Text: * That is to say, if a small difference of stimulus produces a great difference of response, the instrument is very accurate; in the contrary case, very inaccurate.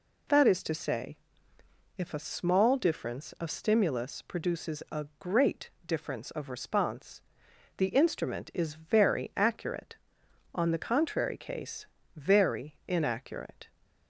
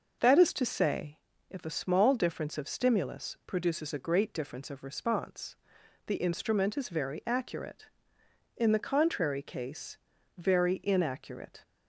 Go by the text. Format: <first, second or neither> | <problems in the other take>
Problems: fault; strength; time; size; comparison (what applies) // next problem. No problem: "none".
second | pauses between "great" and "difference"; slight; at 5.7 s; 0.16 s long // says "on" for "in"; at 10.5 s